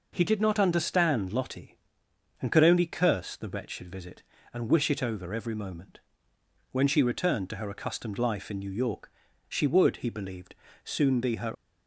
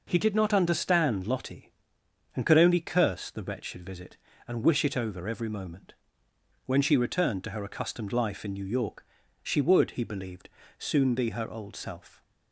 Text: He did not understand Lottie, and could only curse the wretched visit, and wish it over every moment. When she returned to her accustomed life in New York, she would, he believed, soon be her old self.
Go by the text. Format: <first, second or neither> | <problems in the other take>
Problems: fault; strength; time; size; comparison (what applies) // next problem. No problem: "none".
second | stops before "old self"; at 11.5 s